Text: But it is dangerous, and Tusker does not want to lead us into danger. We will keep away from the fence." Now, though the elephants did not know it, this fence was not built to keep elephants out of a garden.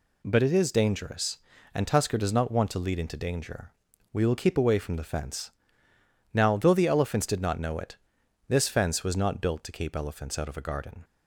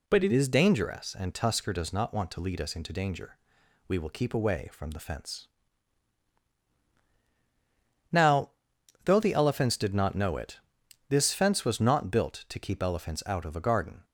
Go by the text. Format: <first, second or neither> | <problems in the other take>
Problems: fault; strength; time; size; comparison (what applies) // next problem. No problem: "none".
second | skips "us"; at 2.9 s